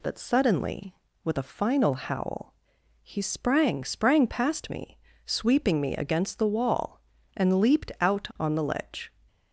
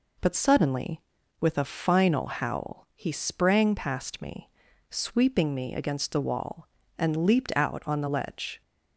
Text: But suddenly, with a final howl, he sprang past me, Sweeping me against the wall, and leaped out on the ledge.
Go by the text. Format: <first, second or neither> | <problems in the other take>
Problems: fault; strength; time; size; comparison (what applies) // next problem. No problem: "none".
second | says "sprang" twice; at 3.8 s